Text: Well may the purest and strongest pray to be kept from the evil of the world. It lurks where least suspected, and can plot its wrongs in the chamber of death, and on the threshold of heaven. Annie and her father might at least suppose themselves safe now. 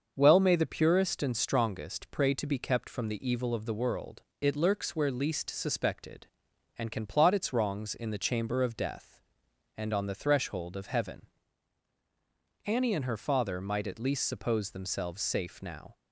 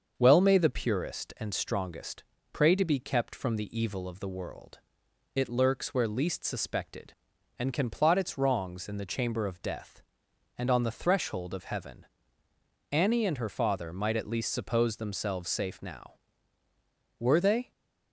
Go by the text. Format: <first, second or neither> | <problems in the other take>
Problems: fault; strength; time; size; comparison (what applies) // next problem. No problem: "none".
first | starts louder than the rest; until 1.1 s; 6.5 dB; also in the first // pauses between "strongest" and "pray"; slight; at 2.2 s; 0.30 s long // goes on to say "Were they"; from 17.1 s on; 0.52 s long